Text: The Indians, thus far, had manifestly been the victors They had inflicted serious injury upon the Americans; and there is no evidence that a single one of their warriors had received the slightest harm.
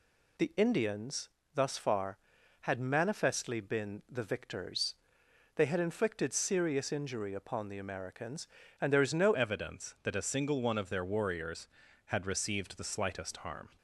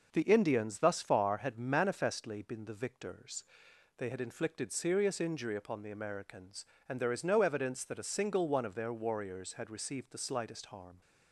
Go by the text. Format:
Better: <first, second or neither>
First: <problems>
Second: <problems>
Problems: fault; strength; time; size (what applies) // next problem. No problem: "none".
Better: second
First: pauses between "victors" and "They"; noticeable; at 4.9 s; 0.60 s long // changes voice at "evidence"; from 9.3 s on; 4.4 s long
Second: pauses between "victors" and "They"; noticeable; at 3.4 s; 0.54 s long